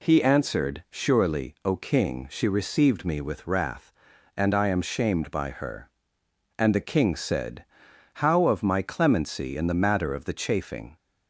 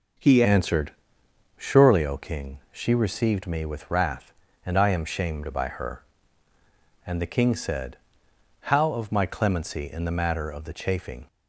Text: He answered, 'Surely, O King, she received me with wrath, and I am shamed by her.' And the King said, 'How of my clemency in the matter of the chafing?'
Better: first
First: none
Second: changes voice at "answered"; from 0.4 s on; 10.8 s long

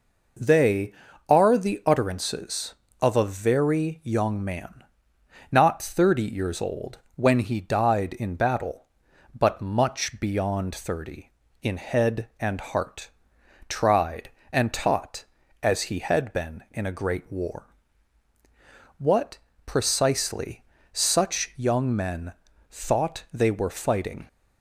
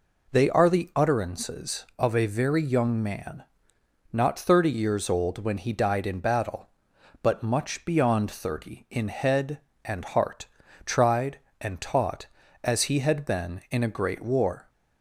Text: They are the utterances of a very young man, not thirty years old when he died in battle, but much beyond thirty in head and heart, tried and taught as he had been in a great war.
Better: second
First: pauses between "old" and "when"; slight; at 6.9 s; 0.16 s long // goes on to say "What precisely such young men thought they were fighting"; strong; from 18.9 s on; 5.2 s long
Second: none

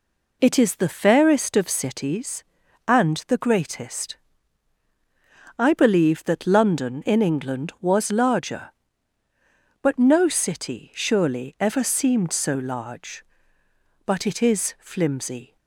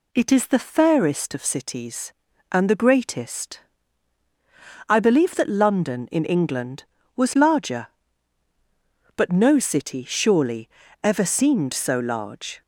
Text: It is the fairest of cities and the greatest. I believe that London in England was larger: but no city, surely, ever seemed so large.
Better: second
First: goes on to say "But it is flimsy"; from 14.0 s on; 1.5 s long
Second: none

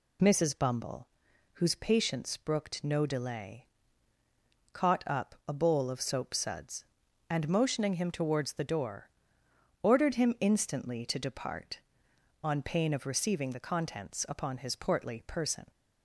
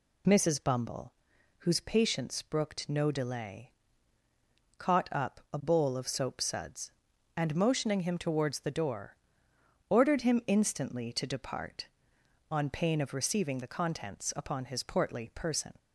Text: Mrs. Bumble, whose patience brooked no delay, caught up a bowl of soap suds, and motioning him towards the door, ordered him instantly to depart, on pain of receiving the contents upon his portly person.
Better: neither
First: none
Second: none

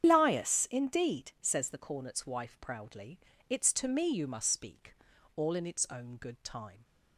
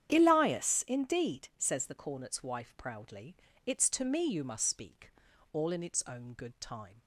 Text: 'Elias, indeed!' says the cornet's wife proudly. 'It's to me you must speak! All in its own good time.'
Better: second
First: loses the start of "Elias"; at 0.0 s; 110 ms // starts louder than the rest; strong; until 1.1 s; 8.5 dB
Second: starts louder than the rest; strong; until 1.1 s; 9 dB

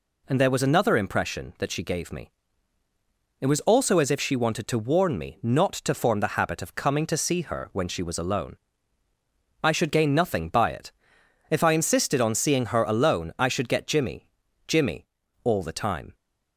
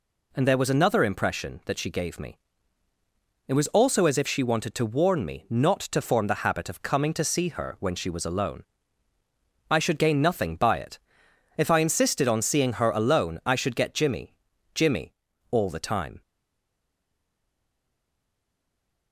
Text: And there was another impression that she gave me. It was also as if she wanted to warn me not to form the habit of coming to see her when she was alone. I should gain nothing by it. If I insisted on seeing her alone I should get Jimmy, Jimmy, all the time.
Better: first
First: none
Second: stays silent after the last word; strong; from 16.2 s on; 2.9 s long

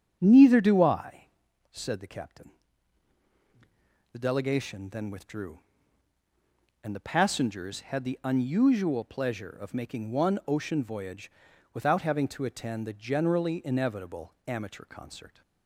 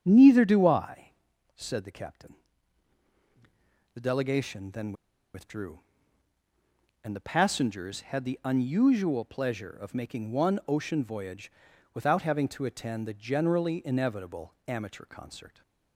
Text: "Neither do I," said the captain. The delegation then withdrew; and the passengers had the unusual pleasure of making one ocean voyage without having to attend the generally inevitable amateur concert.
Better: first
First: starts louder than the rest; strong; until 1.2 s; 7.5 dB // pauses between "voyage" and "without"; at 11.2 s; 0.44 s long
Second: starts louder than the rest; strong; until 1.0 s; 7.5 dB // pauses between "then" and "withdrew"; at 4.9 s; 0.41 s long // pauses between "voyage" and "without"; at 11.4 s; 0.44 s long

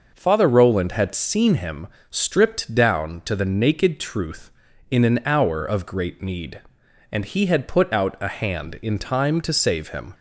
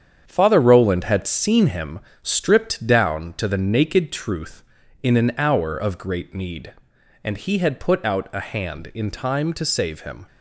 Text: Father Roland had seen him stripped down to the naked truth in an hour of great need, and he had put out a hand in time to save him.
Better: first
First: pauses between "him" and "stripped"; slight; at 1.8 s; 0.20 s long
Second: gets quieter; throughout; 7 dB // pauses between "him" and "stripped"; slight; at 2.0 s; 0.20 s long

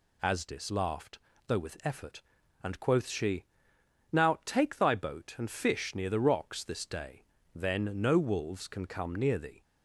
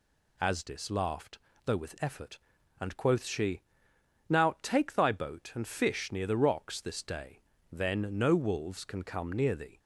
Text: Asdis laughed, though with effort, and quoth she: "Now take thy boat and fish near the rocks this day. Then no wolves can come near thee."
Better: neither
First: none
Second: none

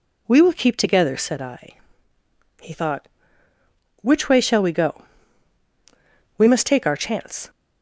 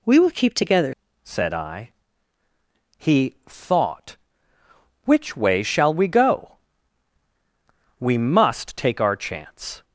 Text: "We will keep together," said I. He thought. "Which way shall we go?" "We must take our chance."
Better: first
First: none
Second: changes voice at "said"; from 1.2 s on; 8.6 s long

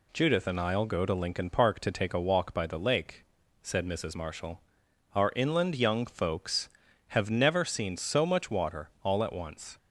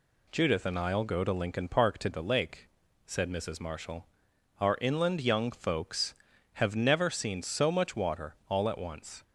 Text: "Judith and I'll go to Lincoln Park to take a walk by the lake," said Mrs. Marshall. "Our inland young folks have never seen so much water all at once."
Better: first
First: none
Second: skips "take a walk by"; at 2.1 s

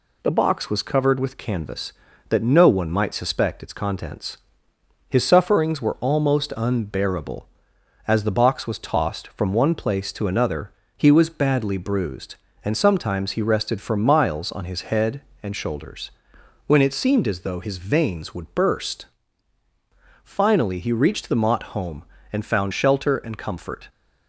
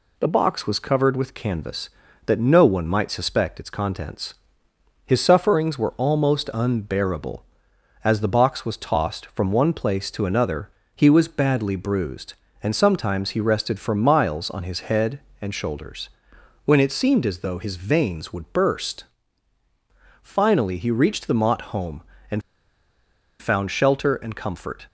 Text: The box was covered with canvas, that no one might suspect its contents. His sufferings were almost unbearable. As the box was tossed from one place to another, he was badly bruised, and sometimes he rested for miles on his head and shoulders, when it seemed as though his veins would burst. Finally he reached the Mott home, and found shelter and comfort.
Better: first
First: none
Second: pauses between "and" and "found"; at 22.4 s; 0.98 s long

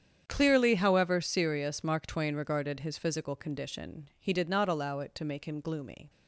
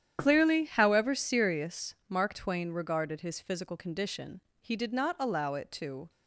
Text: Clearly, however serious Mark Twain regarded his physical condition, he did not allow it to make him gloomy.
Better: first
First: starts louder than the rest; strong; until 1.2 s; 8.5 dB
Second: starts louder than the rest; strong; until 1.2 s; 9.5 dB // pauses between "serious" and "Mark"; slight; at 1.9 s; 0.16 s long // stops before "make him gloomy"; at 6.0 s

